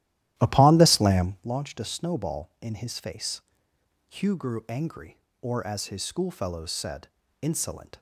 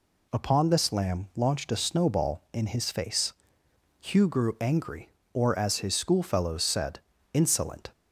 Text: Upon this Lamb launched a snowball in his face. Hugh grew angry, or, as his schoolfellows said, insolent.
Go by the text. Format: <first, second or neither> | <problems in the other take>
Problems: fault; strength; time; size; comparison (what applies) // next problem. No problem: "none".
second | starts louder than the rest; strong; until 1.5 s; 13.5 dB